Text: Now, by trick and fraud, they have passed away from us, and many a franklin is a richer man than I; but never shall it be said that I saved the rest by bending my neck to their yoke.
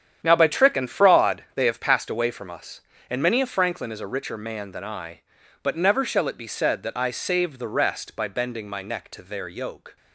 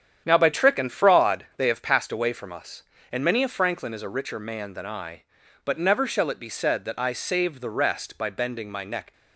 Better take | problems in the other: first | starts louder than the rest; strong; until 1.2 s; 9 dB; strong in the first // stops before "to their yoke"; at 9.1 s

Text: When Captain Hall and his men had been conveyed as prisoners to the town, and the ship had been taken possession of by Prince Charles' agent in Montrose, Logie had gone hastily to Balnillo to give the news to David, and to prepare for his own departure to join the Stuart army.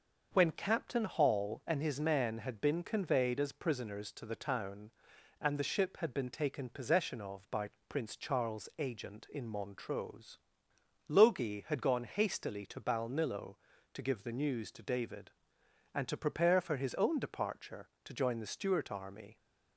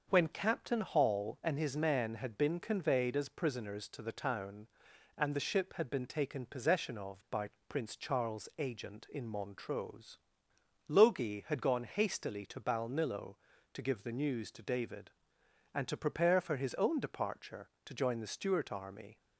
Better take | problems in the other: neither | starts louder than the rest; the same in both // pauses between "by" and "Prince"; slight; the same in both

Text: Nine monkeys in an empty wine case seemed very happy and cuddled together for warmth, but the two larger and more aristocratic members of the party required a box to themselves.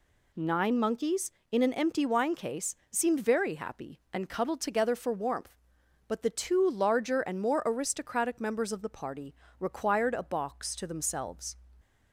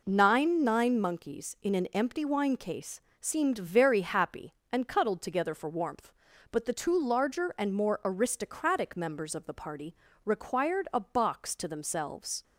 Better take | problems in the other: first | says "Nine" twice; at 0.6 s // pauses between "case" and "seemed"; slight; at 2.9 s; 0.22 s long; slight in the first // pauses between "party" and "required"; slight; at 9.9 s; 0.30 s long; slight in the first

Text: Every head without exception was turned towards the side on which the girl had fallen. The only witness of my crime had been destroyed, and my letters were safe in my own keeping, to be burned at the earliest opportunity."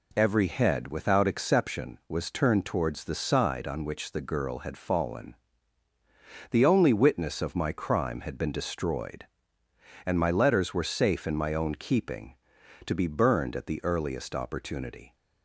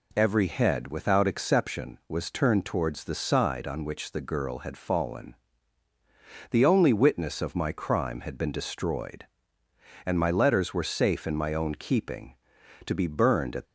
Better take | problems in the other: first | stops before "the earliest opportunity"; at 13.6 s

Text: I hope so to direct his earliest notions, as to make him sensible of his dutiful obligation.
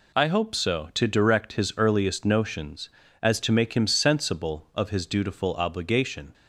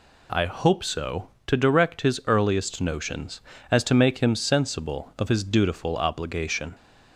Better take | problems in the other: neither | none

